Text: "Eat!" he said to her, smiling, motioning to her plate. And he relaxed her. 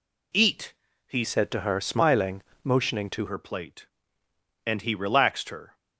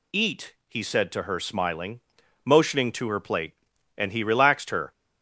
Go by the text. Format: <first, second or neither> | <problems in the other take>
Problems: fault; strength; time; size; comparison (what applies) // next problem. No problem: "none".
second | changes voice from "said" to "to"; from 1.2 to 3.2 s; 2.0 s long